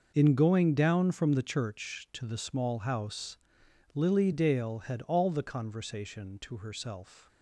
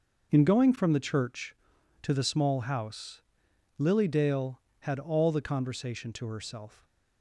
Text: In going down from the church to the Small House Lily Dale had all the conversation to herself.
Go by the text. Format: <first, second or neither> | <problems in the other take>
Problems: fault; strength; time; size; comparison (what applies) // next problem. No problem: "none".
first | starts louder than the rest; noticeable; until 1.3 s; 6 dB // skips "down"; at 0.7 s // pauses between "House" and "Lily"; noticeable; at 3.2 s; 0.58 s long; noticeable in the first